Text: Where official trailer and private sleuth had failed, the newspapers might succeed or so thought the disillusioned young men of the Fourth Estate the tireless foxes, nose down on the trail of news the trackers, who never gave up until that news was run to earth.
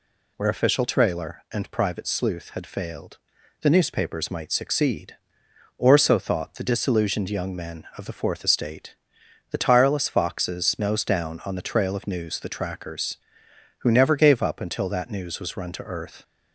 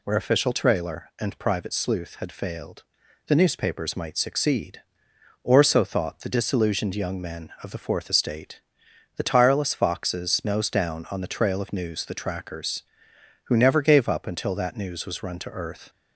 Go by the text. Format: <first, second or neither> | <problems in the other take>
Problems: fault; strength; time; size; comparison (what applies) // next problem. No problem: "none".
neither | pauses between "Estate" and "the"; noticeable; the same in both